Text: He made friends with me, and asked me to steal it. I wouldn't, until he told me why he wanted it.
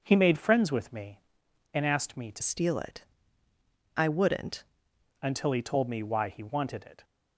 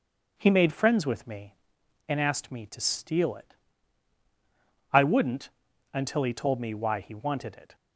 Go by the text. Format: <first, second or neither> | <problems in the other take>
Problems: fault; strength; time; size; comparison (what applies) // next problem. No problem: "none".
second | changes voice from "steal" to "wouldn't"; from 2.4 to 4.6 s; 2.2 s long